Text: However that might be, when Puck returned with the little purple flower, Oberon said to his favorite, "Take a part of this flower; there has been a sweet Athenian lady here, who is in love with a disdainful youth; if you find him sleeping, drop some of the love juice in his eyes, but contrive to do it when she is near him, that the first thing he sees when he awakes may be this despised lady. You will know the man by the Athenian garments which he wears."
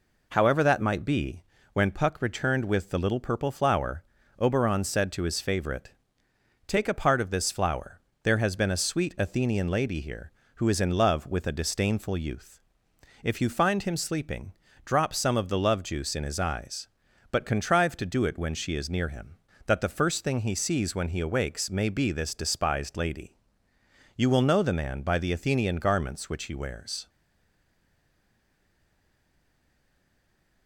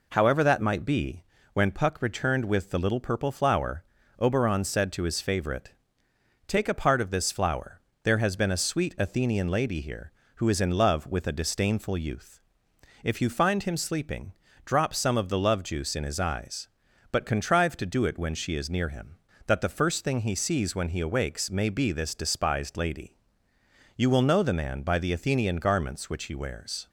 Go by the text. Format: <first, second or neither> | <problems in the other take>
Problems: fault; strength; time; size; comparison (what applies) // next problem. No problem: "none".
second | stays silent after the last word; strong; from 27.0 s on; 3.6 s long